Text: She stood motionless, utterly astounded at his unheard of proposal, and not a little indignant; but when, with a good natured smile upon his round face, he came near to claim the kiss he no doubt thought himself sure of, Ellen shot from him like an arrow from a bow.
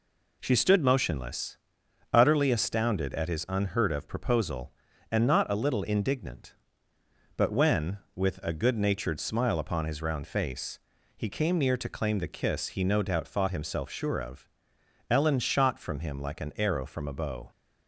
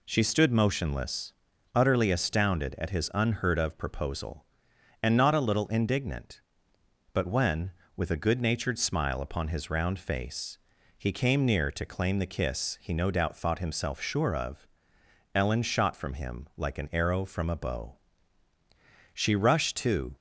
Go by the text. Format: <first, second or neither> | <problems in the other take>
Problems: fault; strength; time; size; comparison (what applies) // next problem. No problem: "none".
first | goes on to say "She rushed to"; noticeable; from 19.1 s on; 1.0 s long